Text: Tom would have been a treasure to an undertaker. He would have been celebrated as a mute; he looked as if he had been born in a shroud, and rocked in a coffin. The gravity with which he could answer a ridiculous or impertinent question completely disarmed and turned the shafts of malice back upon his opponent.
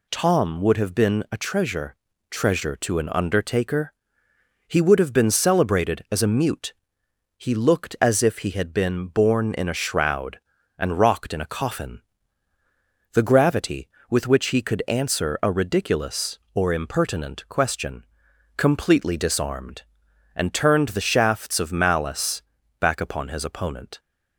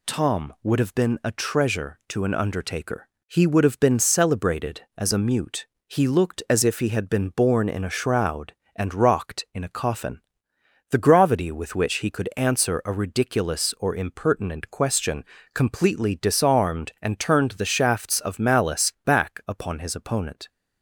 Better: second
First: says "treasure" twice; at 2.2 s // pauses between "question" and "completely"; noticeable; at 18.0 s; 0.50 s long // pauses between "malice" and "back"; at 22.4 s; 0.38 s long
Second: pauses between "question" and "completely"; slight; at 15.2 s; 0.30 s long

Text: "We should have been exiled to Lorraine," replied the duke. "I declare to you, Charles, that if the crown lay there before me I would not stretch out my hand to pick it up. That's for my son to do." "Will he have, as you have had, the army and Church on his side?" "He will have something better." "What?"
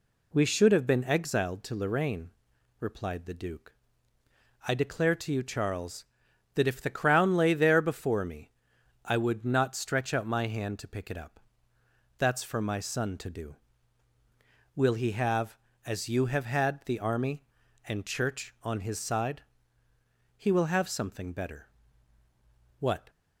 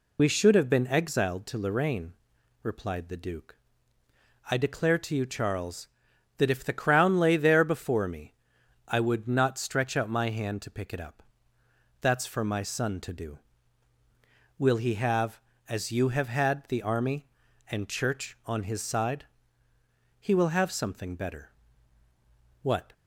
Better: first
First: pauses between "me" and "I"; noticeable; at 8.4 s; 0.54 s long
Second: loses the start of "We"; at 0.1 s; 40 ms // pauses between "me" and "I"; noticeable; at 8.3 s; 0.54 s long

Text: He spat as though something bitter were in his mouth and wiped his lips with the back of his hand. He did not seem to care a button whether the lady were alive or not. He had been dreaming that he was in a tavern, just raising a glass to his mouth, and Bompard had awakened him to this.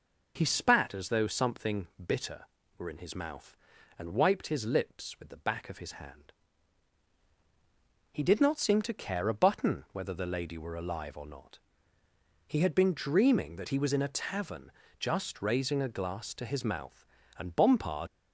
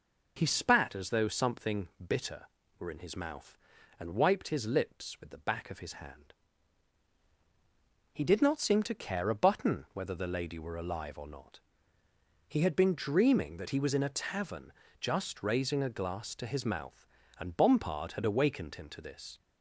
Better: second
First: stops before "had awakened him to this"; at 18.0 s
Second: none

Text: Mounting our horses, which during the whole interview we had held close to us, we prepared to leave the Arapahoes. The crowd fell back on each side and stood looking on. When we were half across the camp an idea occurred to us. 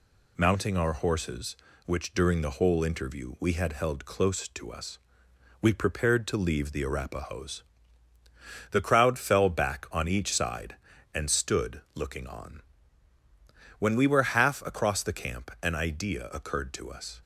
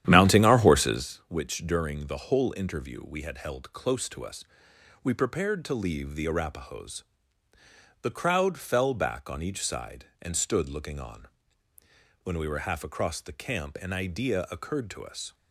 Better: first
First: none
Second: starts louder than the rest; strong; until 1.1 s; 11 dB

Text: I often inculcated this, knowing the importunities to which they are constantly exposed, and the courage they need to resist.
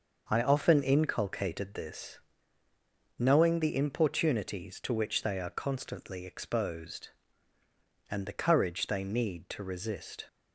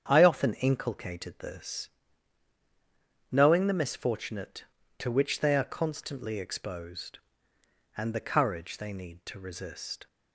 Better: first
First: starts louder than the rest; noticeable; until 1.3 s; 6 dB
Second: starts louder than the rest; strong; until 1.0 s; 8 dB // says "misfortunate" for "importunities"; at 3.7 s

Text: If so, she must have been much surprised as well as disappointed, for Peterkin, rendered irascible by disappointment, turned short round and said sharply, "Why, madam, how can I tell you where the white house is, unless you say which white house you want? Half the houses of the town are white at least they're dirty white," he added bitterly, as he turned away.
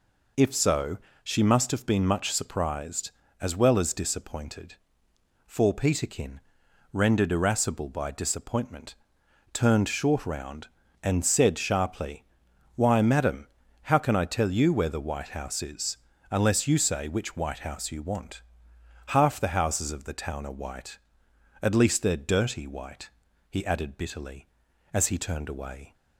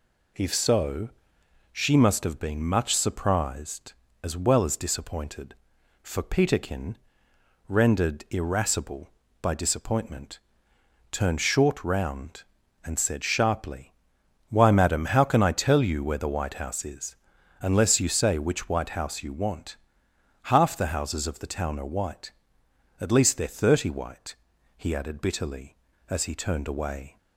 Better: first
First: none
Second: says "thirty" for "dirty"; at 23.5 s

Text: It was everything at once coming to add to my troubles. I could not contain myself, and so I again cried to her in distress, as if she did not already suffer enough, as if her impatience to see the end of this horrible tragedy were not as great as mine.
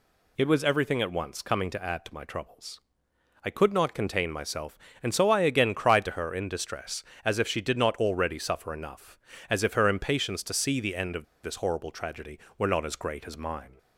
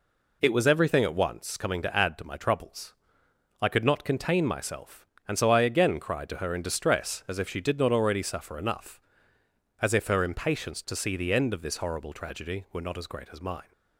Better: second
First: pauses between "of" and "this"; slight; at 11.2 s; 0.20 s long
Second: none

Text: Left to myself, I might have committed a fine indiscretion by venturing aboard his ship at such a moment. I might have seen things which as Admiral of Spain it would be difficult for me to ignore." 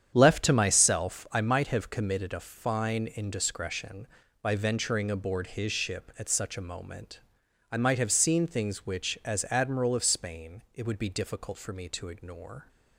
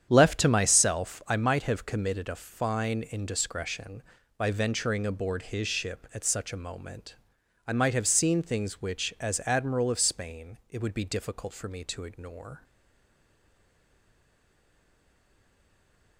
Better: first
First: starts louder than the rest; strong; until 1.1 s; 8.5 dB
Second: starts louder than the rest; strong; until 1.1 s; 8.5 dB // stays silent after the last word; strong; from 12.6 s on; 3.5 s long

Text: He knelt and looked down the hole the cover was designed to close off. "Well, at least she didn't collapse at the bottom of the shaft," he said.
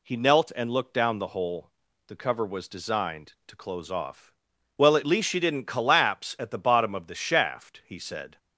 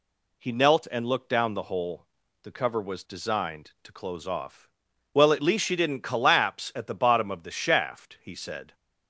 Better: neither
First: pauses between "hole" and "the"; at 1.6 s; 0.38 s long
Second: pauses between "hole" and "the"; at 2.0 s; 0.38 s long

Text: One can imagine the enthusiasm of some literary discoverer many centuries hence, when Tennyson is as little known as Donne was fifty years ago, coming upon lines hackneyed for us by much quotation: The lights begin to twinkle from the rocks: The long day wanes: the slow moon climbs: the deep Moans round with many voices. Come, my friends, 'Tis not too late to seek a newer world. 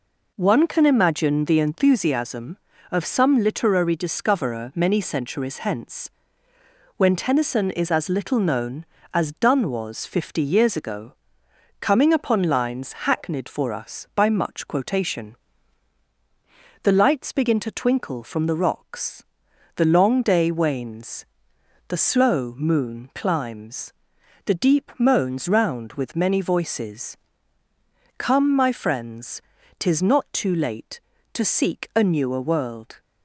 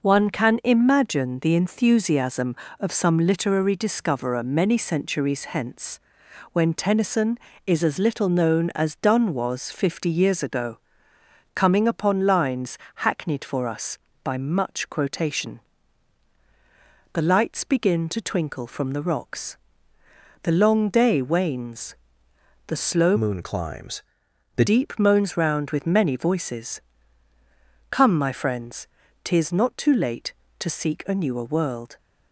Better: first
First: none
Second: pauses between "lines" and "hackneyed"; slight; at 12.7 s; 0.16 s long // changes voice from "moon" to "the"; from 23.1 to 24.6 s; 1.5 s long

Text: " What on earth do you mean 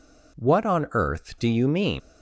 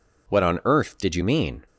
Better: first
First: none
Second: says "did" for "do"; at 0.9 s

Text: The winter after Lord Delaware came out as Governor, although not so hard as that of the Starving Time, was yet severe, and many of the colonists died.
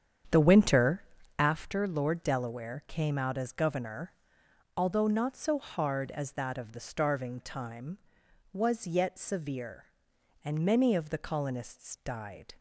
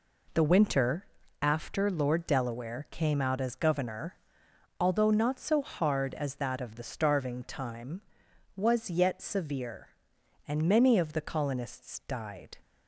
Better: second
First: starts louder than the rest; strong; until 1.6 s; 8 dB // pauses between "winter" and "after"; slight; at 1.0 s; 0.34 s long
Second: pauses between "winter" and "after"; slight; at 1.0 s; 0.34 s long

